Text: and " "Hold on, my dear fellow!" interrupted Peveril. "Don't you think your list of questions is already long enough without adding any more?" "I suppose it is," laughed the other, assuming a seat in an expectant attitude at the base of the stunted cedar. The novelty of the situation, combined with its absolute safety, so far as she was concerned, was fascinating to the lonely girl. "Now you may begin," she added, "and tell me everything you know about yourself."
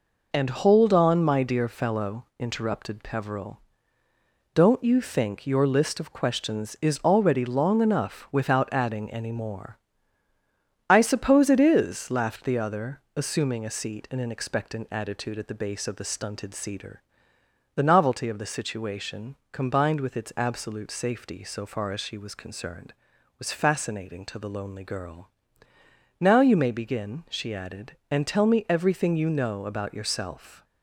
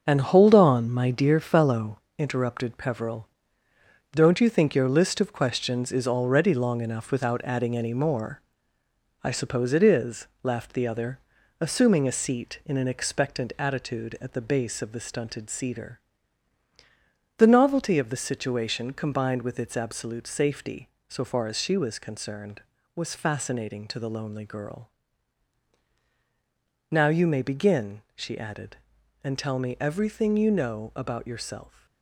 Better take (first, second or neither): first